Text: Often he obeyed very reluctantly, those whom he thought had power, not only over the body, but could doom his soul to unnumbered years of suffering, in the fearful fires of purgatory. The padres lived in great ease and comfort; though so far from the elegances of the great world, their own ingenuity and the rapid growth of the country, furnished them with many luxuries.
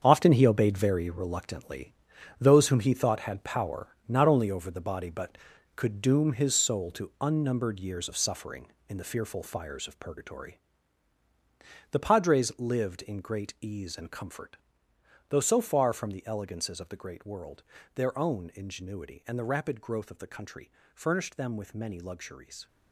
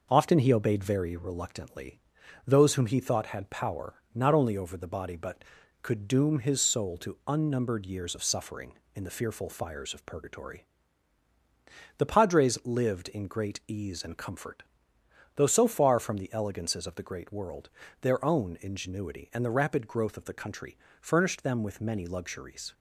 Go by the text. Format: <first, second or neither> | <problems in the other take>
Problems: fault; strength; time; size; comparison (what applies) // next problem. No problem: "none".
second | gets quieter; strong; throughout; 10 dB